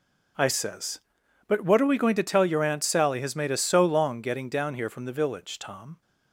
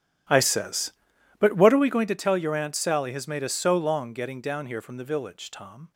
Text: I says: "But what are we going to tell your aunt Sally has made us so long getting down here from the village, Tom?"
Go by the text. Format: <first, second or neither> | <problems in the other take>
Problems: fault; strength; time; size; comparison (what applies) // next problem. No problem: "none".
first | starts louder than the rest; strong; until 2.0 s; 11.5 dB